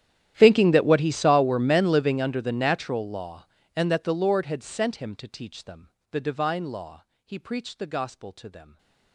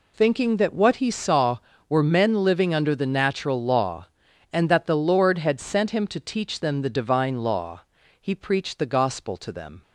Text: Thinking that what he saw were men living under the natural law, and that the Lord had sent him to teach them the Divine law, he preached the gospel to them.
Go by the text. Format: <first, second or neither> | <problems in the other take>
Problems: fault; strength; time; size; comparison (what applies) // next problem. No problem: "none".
second | gets quieter; strong; throughout; 27 dB // pauses between "them" and "the"; slight; at 5.8 s; 0.24 s long // stays silent after the last word; slight; from 8.6 s on; 0.5 s long